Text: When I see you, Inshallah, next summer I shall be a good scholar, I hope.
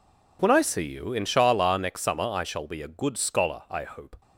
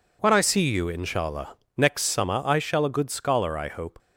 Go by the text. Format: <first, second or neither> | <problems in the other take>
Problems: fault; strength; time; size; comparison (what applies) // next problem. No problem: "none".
first | skips "be"; at 2.8 s